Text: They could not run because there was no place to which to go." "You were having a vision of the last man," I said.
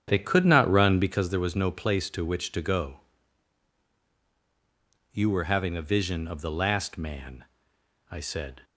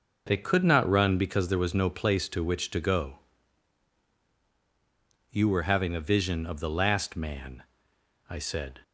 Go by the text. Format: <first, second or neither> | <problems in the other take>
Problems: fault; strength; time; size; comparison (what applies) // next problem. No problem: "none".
second | starts louder than the rest; strong; until 1.3 s; 8.5 dB